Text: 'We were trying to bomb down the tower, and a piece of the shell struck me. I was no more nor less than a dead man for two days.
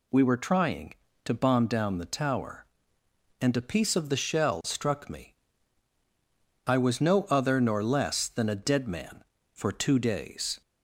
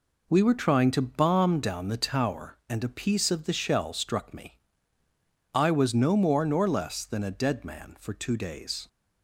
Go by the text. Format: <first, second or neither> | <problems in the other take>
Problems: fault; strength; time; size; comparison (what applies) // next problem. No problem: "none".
second | says "other" for "more"; at 7.2 s